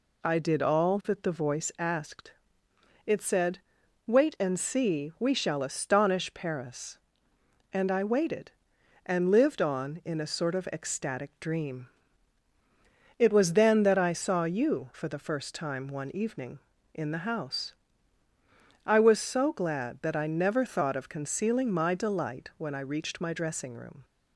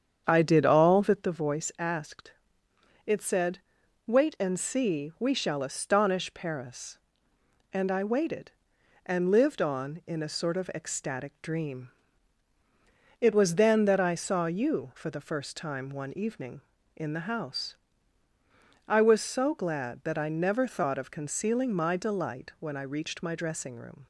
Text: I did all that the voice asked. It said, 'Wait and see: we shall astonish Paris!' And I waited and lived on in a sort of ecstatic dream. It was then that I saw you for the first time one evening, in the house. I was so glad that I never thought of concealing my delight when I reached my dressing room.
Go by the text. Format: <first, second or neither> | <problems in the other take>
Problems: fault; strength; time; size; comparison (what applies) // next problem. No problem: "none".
first | starts louder than the rest; strong; until 1.2 s; 8 dB